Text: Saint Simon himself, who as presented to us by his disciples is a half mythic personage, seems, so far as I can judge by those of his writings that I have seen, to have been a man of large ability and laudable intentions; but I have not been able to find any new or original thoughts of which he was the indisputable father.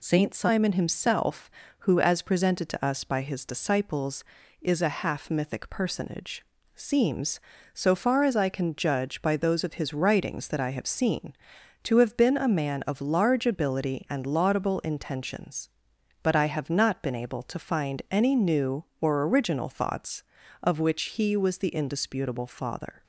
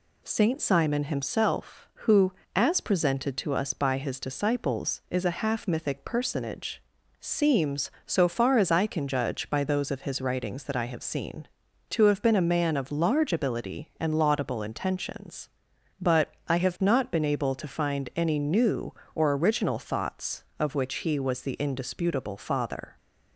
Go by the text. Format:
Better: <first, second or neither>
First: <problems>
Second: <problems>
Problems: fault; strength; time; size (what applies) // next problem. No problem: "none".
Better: neither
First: none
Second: none